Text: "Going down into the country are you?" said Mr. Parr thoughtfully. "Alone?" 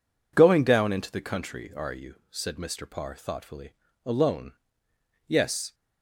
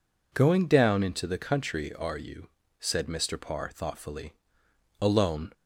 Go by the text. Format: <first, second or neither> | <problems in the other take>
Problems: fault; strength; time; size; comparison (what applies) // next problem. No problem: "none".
second | goes on to say "Yes"; slight; from 5.2 s on; 0.46 s long